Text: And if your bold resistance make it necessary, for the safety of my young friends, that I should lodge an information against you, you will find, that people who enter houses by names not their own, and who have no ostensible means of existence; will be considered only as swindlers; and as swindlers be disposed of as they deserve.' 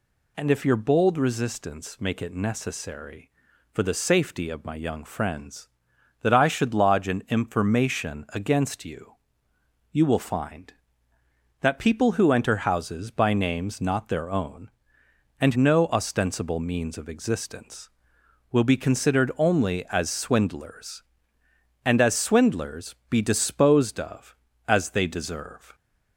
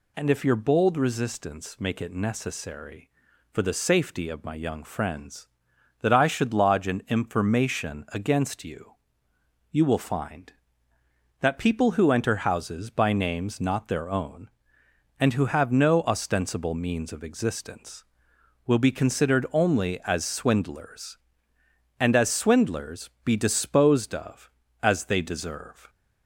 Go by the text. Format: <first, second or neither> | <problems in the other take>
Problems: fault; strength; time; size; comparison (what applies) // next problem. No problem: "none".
second | skips "who have"; at 15.5 s // pauses between "swindlers" and "be"; slight; at 22.9 s; 0.16 s long; slight in the second